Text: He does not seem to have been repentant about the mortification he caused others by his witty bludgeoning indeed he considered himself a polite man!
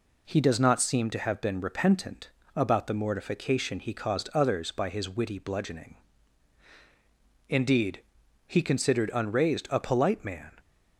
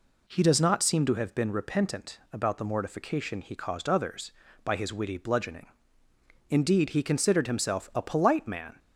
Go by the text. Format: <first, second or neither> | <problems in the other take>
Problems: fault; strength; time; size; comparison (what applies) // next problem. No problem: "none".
second | pauses between "repentant" and "about"; slight; at 2.2 s; 0.26 s long // pauses between "bludgeoning" and "indeed"; strong; at 5.9 s; 1.5 s long; noticeable in the second // pauses between "indeed" and "he"; noticeable; at 8.0 s; 0.46 s long // says "unraised" for "himself"; at 9.1 s